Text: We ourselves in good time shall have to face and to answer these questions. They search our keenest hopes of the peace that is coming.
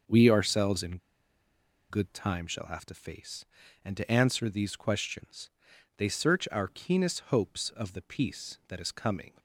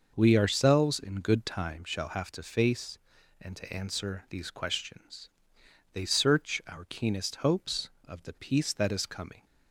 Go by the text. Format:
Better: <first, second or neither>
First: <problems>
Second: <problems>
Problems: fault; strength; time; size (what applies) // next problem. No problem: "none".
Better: second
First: pauses between "in" and "good"; noticeable; at 0.9 s; 0.93 s long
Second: none